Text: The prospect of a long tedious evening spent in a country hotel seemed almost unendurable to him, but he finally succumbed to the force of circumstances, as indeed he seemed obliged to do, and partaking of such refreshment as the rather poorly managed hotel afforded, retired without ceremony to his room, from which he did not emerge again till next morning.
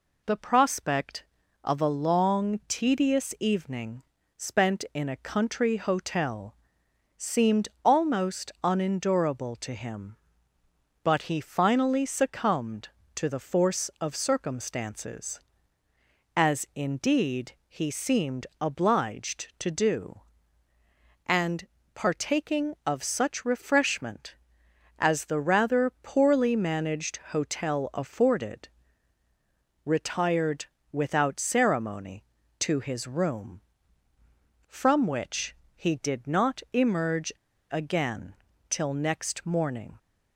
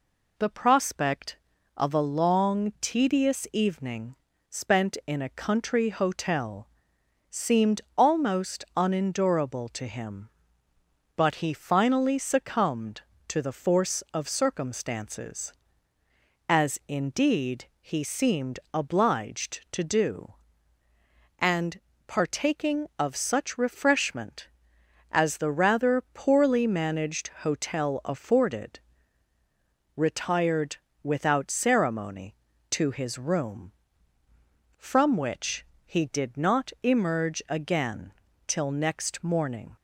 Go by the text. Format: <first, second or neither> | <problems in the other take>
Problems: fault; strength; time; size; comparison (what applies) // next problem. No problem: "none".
second | pauses between "evening" and "spent"; slight; at 4.0 s; 0.34 s long; slight in the second // pauses between "hotel" and "seemed"; noticeable; at 6.5 s; 0.62 s long; noticeable in the second // pauses between "seemed" and "almost"; slight; at 7.6 s; 0.16 s long; slight in the second // pauses between "indeed" and "he"; slight; at 17.5 s; 0.16 s long; slight in the second // pauses between "seemed" and "obliged"; slight; at 18.4 s; 0.16 s long; slight in the second // pauses between "and" and "partaking"; slight; at 21.6 s; 0.26 s long; slight in the second // pauses between "retired" and "without"; slight; at 30.6 s; 0.30 s long; slight in the second // pauses between "which" and "he"; slight; at 35.5 s; 0.22 s long; slight in the second // pauses between "emerge" and "again"; at 37.3 s; 0.36 s long // pauses between "again" and "till"; slight; at 38.3 s; 0.36 s long; slight in the second